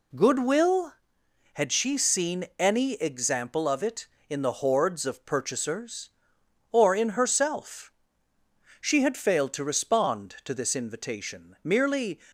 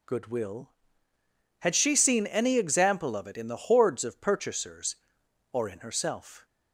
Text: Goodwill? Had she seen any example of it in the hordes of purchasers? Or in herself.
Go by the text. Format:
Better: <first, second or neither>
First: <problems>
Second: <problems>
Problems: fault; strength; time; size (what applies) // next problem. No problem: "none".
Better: second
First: goes on to say "She had failed to respond to this invitation merely"; strong; from 8.8 s on; 3.3 s long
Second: none